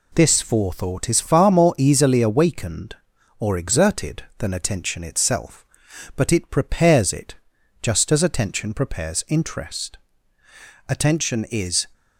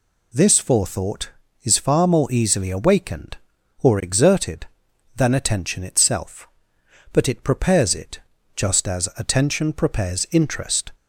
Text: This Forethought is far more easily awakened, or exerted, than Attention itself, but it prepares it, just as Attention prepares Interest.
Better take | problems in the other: second | goes on to say "Attention is"; noticeable; from 10.8 s on; 0.98 s long

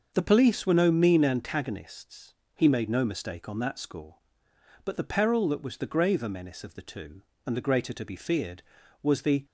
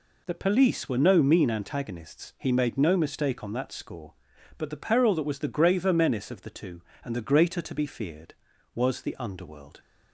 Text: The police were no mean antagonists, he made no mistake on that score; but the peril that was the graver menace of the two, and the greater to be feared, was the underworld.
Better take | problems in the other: second | starts louder than the rest; until 1.1 s; 6.5 dB // stops before "underworld"; at 9.4 s

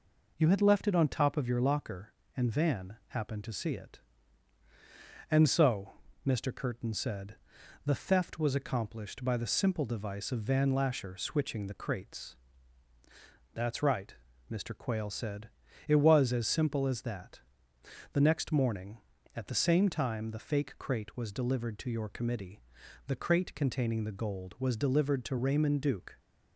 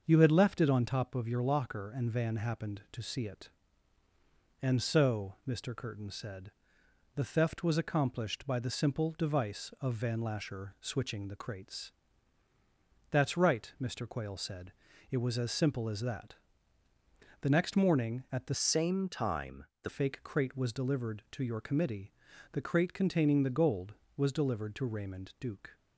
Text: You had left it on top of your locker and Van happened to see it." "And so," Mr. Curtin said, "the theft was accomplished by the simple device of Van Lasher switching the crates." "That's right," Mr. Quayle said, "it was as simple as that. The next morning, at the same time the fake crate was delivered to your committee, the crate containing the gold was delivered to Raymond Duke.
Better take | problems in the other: first | starts louder than the rest; until 1.0 s; 6.5 dB // changes voice from "same" to "the"; from 18.5 to 19.8 s; 1.3 s long // pauses between "time" and "the"; slight; at 19.6 s; 0.16 s long

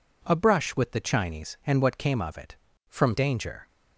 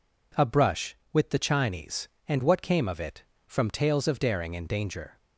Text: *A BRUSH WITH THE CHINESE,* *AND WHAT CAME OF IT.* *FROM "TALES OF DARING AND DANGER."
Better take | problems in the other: second | skips "TALES OF DARING AND"; at 3.1 s

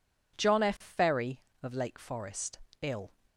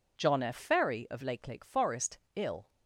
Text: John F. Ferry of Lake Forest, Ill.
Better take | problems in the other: first | says "Lake" twice; at 1.4 s

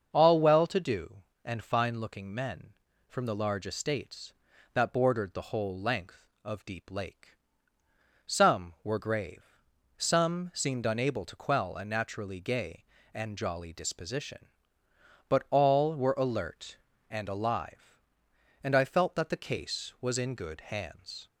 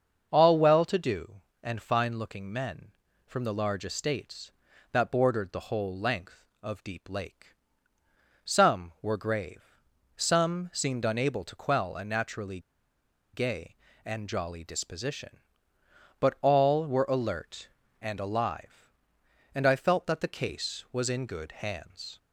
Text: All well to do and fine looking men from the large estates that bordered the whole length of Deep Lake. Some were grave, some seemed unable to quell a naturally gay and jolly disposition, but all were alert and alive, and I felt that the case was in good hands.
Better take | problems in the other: first | starts louder than the rest; until 1.3 s; 6.5 dB; also in the first // pauses between "naturally" and "gay"; noticeable; at 12.5 s; 0.74 s long

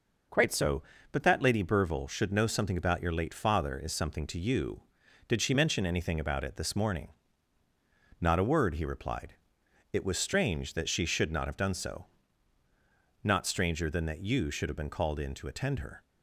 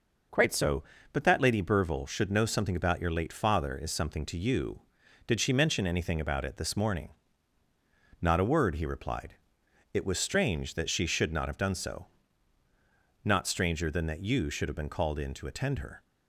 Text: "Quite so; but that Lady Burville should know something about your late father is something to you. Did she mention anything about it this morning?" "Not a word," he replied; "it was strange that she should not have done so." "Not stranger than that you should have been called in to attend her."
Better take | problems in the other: neither | none

